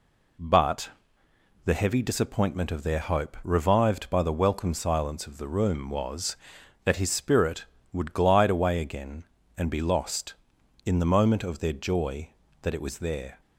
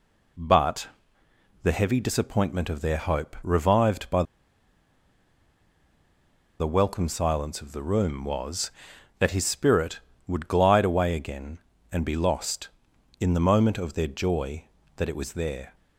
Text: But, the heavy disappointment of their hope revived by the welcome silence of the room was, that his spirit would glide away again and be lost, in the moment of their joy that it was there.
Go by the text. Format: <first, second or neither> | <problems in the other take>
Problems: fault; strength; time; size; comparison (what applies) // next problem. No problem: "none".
first | pauses between "by" and "the"; strong; at 4.2 s; 2.3 s long